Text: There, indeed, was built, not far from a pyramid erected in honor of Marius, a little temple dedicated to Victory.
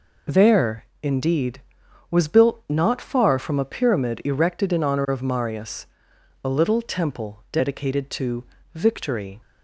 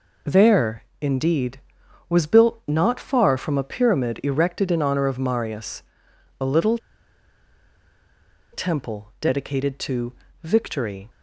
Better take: first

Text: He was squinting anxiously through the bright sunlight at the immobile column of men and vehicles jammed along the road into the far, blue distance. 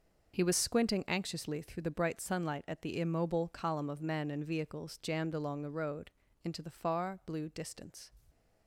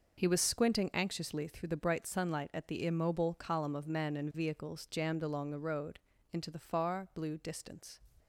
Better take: neither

